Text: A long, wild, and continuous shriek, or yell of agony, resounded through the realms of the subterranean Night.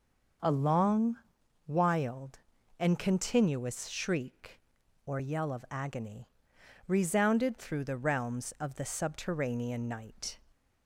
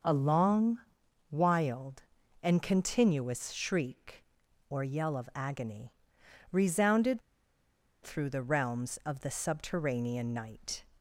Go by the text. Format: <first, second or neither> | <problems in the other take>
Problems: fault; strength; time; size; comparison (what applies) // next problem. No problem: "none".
first | starts louder than the rest; until 1.5 s; 6.5 dB; also in the first // pauses between "resounded" and "through"; noticeable; at 7.2 s; 0.81 s long